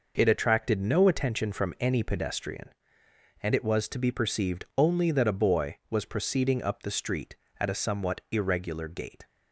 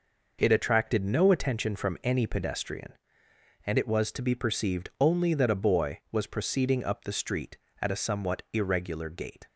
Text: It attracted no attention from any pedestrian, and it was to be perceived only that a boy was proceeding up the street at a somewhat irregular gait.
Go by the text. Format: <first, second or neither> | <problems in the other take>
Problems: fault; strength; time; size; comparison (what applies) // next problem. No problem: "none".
neither | none